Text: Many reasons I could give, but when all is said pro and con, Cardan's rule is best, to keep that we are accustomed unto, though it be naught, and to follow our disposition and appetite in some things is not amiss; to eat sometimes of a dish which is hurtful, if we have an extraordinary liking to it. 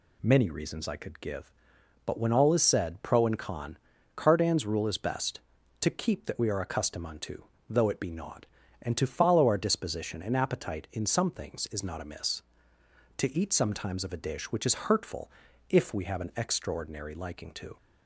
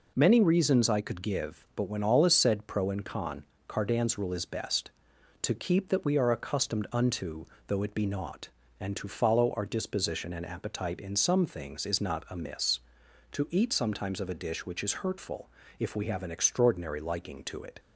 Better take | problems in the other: second | stops before "it"; at 17.7 s

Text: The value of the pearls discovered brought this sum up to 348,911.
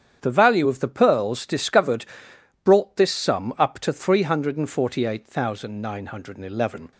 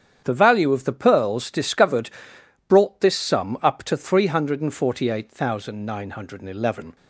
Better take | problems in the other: neither | starts louder than the rest; strong; the same in both // pauses between "discovered" and "brought"; noticeable; the same in both

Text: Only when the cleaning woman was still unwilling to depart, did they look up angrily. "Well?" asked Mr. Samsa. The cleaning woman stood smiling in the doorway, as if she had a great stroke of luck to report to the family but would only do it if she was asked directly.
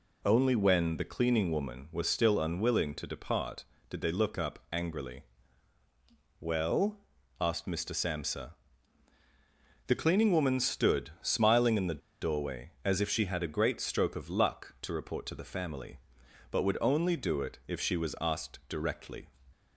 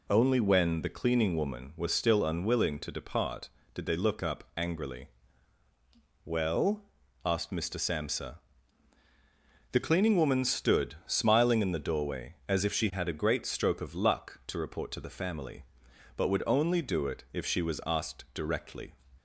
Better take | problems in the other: second | pauses between "the" and "doorway"; slight; at 12.0 s; 0.23 s long

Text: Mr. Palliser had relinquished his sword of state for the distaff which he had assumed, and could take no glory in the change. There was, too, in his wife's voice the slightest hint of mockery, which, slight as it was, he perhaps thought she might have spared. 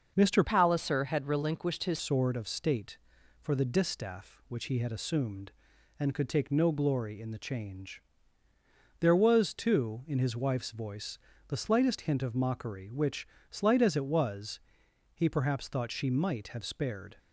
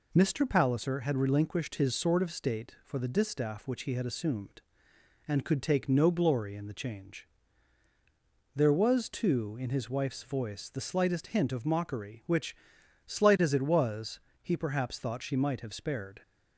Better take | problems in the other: second | starts louder than the rest; until 1.1 s; 6.5 dB // changes voice from "Palliser" to "his"; from 0.4 to 1.9 s; 1.5 s long // pauses between "voice" and "the"; slight; at 11.1 s; 0.30 s long

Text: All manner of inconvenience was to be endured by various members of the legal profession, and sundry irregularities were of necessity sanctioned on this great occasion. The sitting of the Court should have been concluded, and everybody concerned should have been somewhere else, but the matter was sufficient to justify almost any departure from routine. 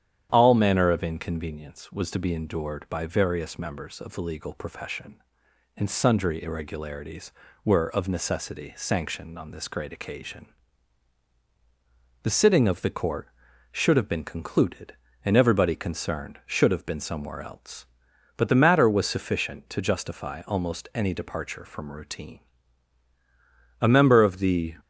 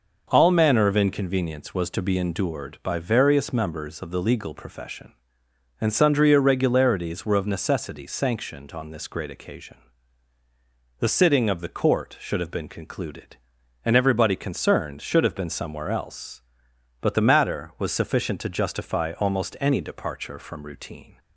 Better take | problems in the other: second | starts louder than the rest; strong; until 1.3 s; 9.5 dB // goes on to say "A member of the"; noticeable; from 23.7 s on; 0.96 s long

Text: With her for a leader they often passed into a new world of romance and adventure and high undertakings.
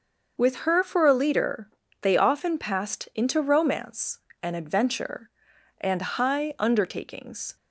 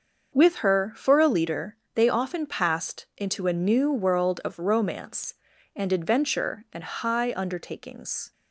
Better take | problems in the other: second | starts louder than the rest; until 1.5 s; 6 dB; also in the second // pauses between "leader" and "they"; slight; at 1.6 s; 0.32 s long; slight in the second // skips "a new world of"; at 3.3 s

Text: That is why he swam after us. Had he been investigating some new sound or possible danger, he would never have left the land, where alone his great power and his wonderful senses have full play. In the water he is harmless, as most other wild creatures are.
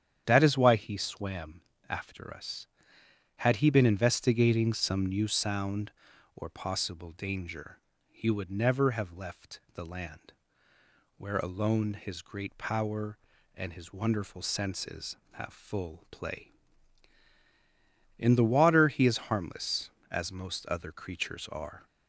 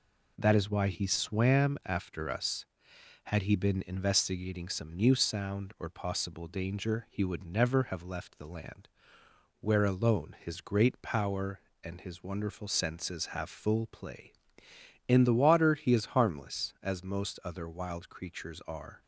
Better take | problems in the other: second | starts louder than the rest; strong; until 1.2 s; 9 dB // pauses between "swam" and "after"; slight; at 1.6 s; 0.28 s long // pauses between "left" and "the"; slight; at 9.5 s; 0.16 s long // skips "wild"; at 20.9 s

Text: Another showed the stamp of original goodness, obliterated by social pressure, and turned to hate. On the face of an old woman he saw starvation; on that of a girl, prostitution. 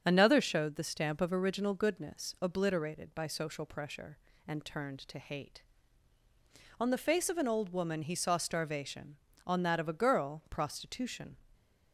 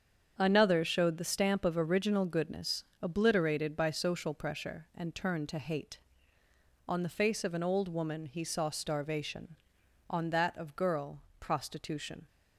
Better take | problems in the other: first | starts louder than the rest; strong; until 1.3 s; 7.5 dB; strong in the first // skips "a"; at 10.7 s

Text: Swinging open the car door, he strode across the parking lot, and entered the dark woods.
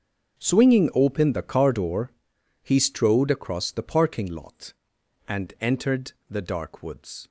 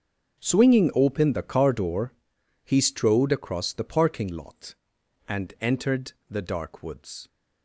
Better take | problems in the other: neither | starts louder than the rest; the same in both // pauses between "entered" and "the"; slight; the same in both

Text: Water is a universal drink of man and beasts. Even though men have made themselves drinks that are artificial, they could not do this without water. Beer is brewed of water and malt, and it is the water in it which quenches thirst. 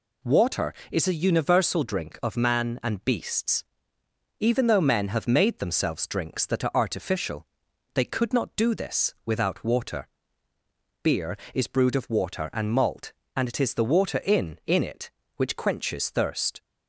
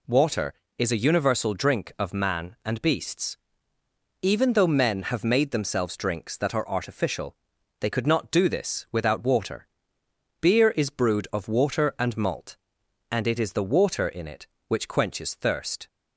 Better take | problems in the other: second | says "in" twice; at 14.6 s

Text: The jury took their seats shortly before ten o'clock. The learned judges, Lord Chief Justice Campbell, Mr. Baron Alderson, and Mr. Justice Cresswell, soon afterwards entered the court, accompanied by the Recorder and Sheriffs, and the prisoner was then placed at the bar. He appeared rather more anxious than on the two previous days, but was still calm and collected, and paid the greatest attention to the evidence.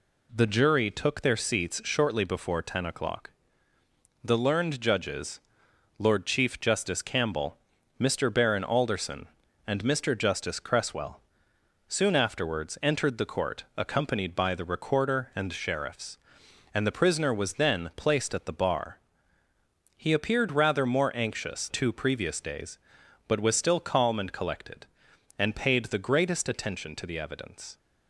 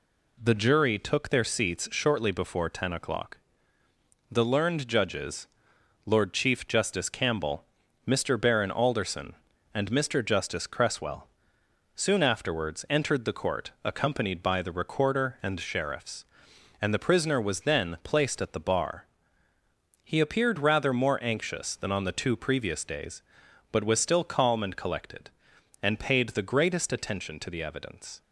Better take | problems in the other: second | skips "than on the"; at 21.6 s

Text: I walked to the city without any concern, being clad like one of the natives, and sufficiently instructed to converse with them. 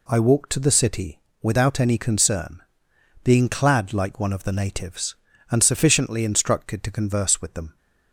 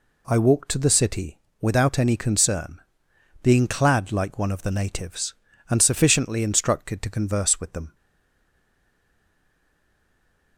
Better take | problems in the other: first | pauses between "city" and "without"; slight; at 1.3 s; 0.24 s long; slight in the first // stays silent after the last word; strong; from 7.9 s on; 2.6 s long

